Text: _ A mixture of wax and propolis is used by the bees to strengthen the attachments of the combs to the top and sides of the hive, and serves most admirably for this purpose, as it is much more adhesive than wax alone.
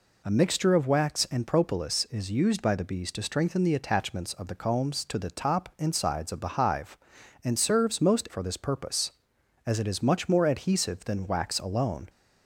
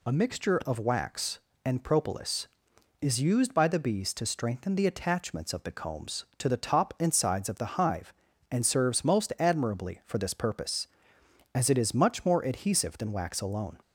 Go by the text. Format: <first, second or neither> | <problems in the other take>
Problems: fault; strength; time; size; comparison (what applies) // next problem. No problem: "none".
second | skips "admirably"; at 8.2 s